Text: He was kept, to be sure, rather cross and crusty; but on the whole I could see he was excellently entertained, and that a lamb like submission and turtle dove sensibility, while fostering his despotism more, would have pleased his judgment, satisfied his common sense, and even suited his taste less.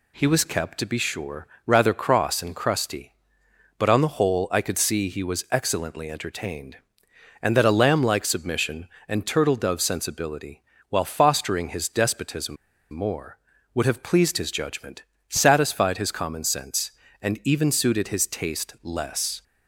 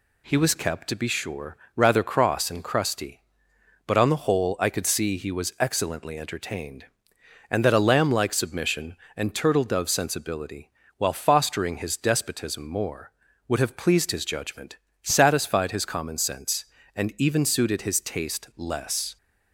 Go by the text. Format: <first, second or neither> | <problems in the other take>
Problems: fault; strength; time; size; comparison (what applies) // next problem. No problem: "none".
second | pauses between "despotism" and "more"; slight; at 12.5 s; 0.34 s long